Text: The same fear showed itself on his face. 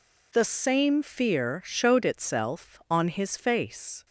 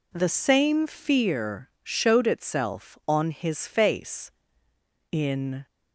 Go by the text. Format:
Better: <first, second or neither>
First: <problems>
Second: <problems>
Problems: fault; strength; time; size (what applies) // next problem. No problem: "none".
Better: first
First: none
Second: goes on to say "In"; from 5.0 s on; 0.56 s long